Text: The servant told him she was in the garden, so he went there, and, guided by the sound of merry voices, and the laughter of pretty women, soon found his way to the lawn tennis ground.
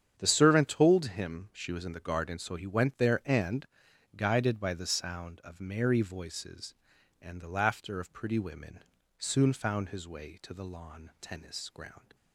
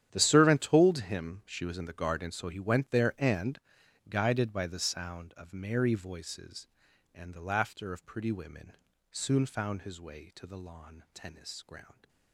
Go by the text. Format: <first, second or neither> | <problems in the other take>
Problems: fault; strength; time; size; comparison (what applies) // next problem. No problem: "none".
first | gets quieter; strong; throughout; 16 dB // starts louder than the rest; strong; until 1.1 s; 10 dB; strong in the first